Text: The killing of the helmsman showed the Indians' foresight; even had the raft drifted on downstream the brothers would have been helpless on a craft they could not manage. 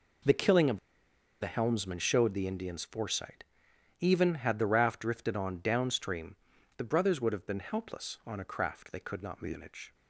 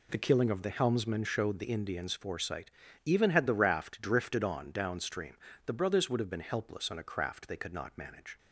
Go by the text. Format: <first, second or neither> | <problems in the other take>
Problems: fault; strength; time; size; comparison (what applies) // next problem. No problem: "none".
second | pauses between "of" and "the"; noticeable; at 0.7 s; 0.62 s long // pauses between "downstream" and "the"; at 6.3 s; 0.40 s long; slight in the second